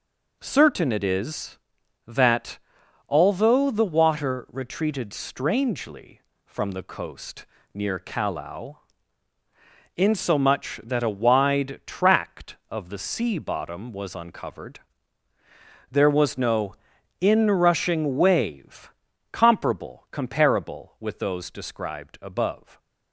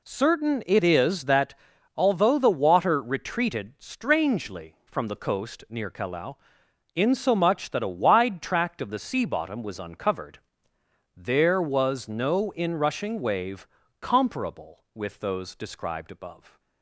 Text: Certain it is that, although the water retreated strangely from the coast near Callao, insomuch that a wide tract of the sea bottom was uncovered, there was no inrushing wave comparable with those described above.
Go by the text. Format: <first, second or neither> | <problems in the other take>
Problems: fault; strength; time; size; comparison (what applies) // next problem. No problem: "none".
second | pauses between "coast" and "near"; slight; at 7.4 s; 0.30 s long // pauses between "no" and "inrushing"; noticeable; at 16.7 s; 0.46 s long // pauses between "wave" and "comparable"; at 18.9 s; 0.40 s long; slight in the second // says "comparable" twice; at 20.1 s